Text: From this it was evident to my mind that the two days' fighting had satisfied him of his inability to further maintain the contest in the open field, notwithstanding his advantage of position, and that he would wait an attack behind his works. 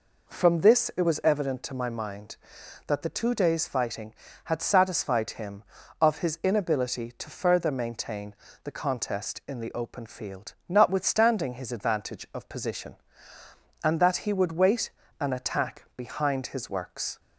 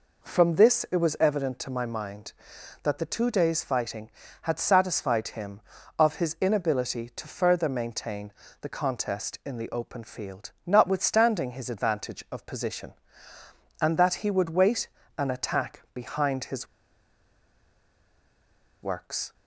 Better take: first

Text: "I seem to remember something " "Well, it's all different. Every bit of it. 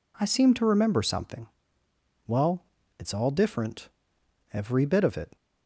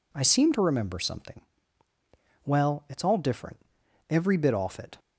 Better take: first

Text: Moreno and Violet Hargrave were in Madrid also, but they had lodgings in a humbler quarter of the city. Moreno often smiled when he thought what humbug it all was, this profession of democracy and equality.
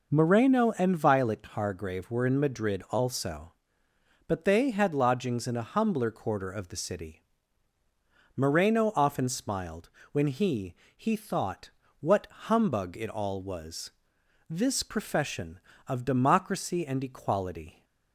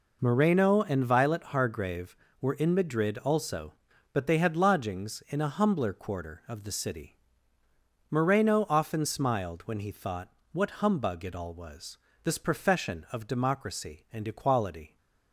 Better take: second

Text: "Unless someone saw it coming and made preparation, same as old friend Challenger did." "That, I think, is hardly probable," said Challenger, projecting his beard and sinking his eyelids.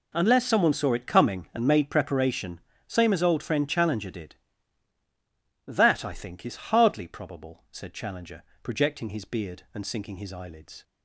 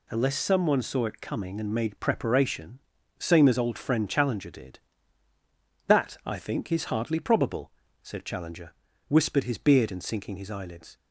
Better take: first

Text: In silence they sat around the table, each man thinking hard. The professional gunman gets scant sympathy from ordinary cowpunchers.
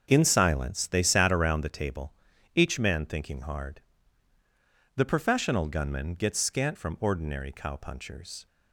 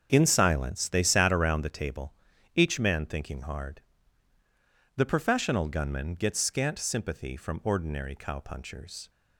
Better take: second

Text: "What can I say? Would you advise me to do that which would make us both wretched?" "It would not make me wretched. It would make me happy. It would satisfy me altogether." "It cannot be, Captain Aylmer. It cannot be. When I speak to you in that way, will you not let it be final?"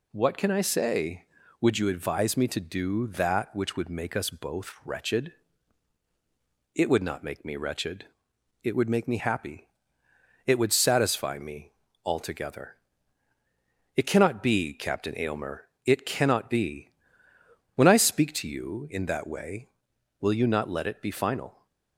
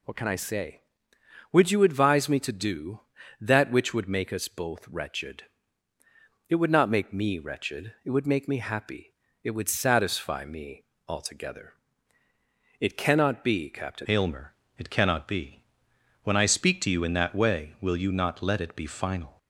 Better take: first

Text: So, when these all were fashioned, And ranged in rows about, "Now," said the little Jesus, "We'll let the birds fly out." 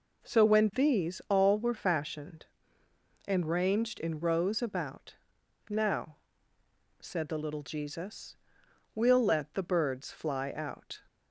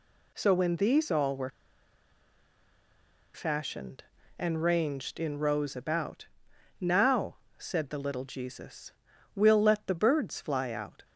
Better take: first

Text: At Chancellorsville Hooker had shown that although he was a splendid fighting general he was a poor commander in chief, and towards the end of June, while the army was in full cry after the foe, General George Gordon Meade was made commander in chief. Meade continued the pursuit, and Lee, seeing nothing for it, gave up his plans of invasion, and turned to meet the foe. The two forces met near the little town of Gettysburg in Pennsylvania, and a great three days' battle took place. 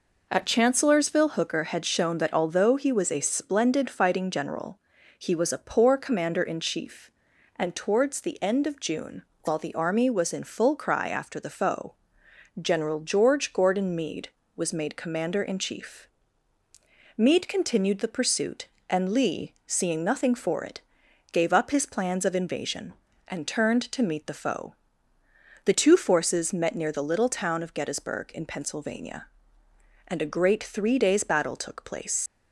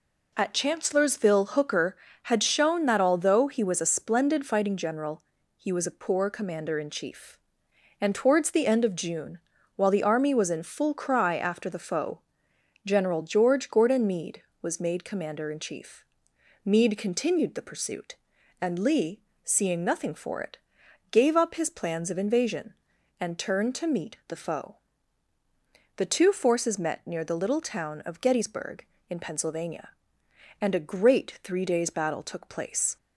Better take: second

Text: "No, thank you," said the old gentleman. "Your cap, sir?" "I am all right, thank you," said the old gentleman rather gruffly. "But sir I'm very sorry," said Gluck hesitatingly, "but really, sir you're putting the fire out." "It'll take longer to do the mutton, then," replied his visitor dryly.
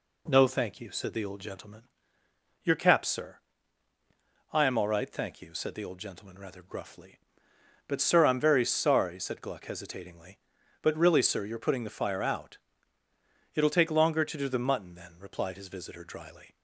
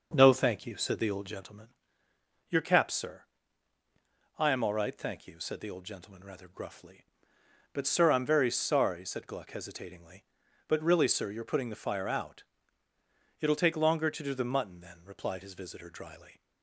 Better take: first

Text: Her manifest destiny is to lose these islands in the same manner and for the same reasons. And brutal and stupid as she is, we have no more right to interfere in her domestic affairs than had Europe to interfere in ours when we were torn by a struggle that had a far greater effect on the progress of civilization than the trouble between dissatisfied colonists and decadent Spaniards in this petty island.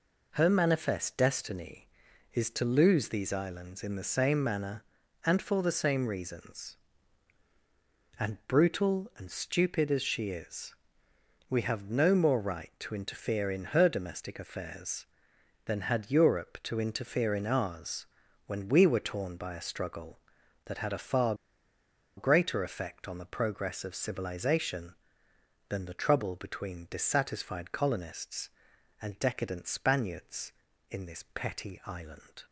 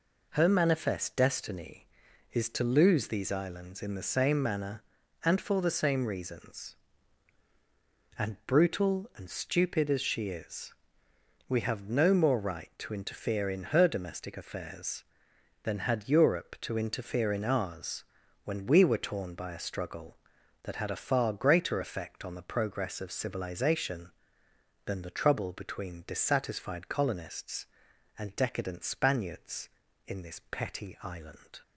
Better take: second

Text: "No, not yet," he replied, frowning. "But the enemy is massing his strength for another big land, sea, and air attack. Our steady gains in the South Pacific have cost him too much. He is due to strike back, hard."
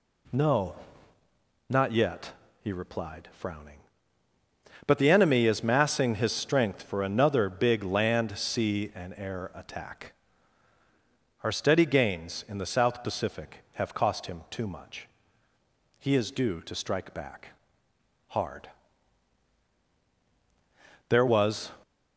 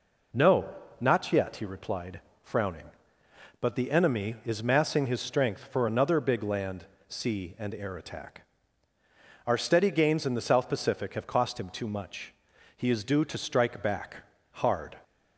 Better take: second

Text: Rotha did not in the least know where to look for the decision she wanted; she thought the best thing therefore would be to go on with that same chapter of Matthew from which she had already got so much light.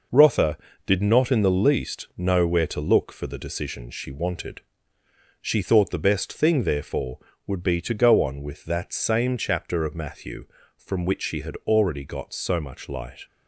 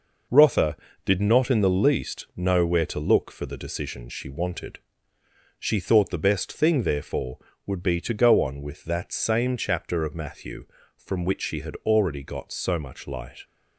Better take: neither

